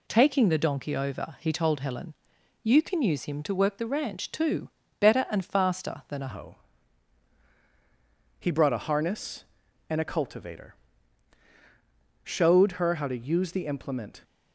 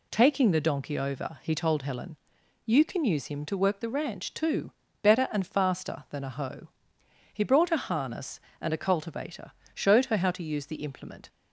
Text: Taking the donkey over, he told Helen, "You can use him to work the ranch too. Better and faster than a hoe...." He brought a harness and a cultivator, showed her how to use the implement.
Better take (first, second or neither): second